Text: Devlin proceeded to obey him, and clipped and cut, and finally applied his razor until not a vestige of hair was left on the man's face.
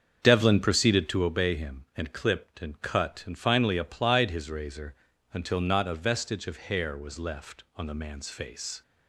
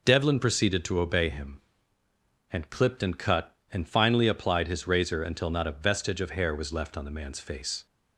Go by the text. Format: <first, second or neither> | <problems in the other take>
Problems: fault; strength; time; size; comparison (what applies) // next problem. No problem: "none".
second | starts louder than the rest; until 1.3 s; 7 dB // pauses between "razor" and "until"; slight; at 4.9 s; 0.36 s long